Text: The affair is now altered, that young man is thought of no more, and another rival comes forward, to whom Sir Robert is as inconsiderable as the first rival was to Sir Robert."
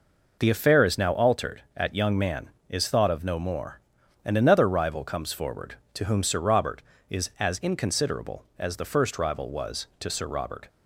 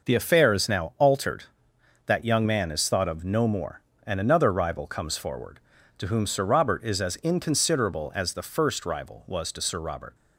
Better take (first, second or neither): second